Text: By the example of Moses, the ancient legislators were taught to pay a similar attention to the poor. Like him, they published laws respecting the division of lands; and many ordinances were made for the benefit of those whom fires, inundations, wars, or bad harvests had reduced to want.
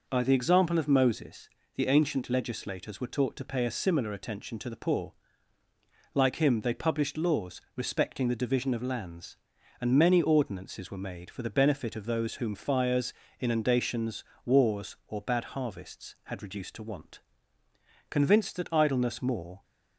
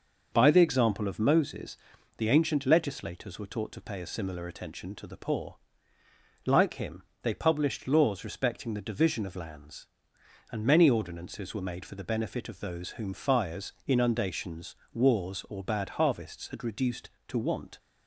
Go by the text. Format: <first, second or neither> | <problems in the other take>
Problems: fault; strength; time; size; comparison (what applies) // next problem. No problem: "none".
second | goes on to say "Convinced that idleness more"; from 18.0 s on; 1.5 s long